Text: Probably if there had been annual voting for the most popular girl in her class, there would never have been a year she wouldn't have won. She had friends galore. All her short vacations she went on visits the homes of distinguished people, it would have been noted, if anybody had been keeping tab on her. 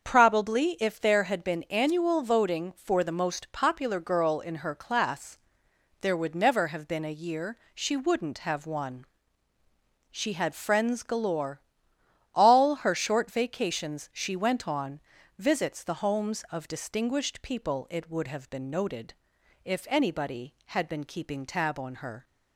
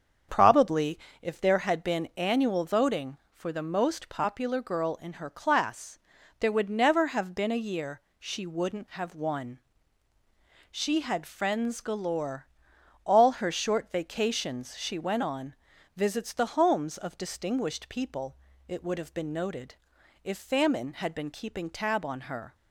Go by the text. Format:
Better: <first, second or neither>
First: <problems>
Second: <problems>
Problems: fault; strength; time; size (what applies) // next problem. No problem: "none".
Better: first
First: starts louder than the rest; until 1.1 s; 7 dB // pauses between "year" and "she"; slight; at 7.5 s; 0.16 s long // pauses between "on" and "visits"; at 15.0 s; 0.38 s long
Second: starts louder than the rest; strong; until 1.5 s; 7 dB // pauses between "Probably" and "if"; slight; at 0.9 s; 0.24 s long // pauses between "year" and "she"; slight; at 8.0 s; 0.18 s long // pauses between "on" and "visits"; at 15.5 s; 0.42 s long // says "famine" for "anybody"; at 20.3 s